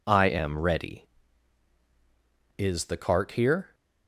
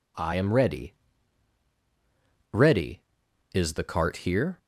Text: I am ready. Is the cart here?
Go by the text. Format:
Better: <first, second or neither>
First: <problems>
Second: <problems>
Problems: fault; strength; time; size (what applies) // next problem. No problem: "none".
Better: first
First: none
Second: says "ready" twice; at 2.5 s